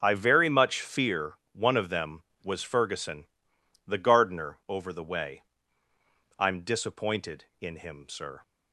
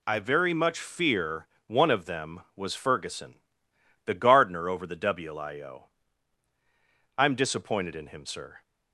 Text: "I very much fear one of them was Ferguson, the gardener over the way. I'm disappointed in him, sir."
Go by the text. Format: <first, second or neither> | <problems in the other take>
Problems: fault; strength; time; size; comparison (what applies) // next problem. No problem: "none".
first | pauses between "fear" and "one"; slight; at 1.4 s; 0.22 s long; slight in the first // says "wlio" for "way"; at 4.9 s